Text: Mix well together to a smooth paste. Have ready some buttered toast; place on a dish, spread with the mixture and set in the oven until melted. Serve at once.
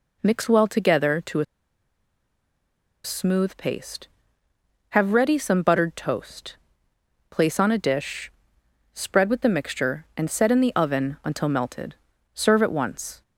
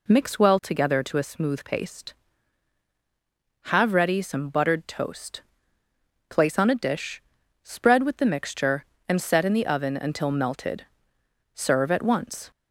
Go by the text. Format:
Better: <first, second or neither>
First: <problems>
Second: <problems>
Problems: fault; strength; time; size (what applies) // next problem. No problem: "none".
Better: second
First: pauses between "a" and "smooth"; strong; at 1.4 s; 1.5 s long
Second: none